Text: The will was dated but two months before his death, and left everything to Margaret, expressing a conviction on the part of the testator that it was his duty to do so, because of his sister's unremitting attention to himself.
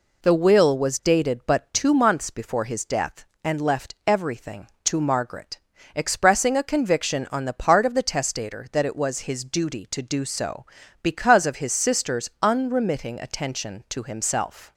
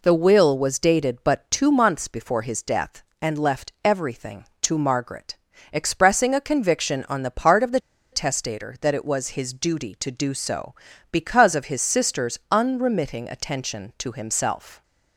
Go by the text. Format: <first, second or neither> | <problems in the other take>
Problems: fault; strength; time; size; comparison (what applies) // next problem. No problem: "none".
first | pauses between "the" and "testator"; slight; at 7.7 s; 0.33 s long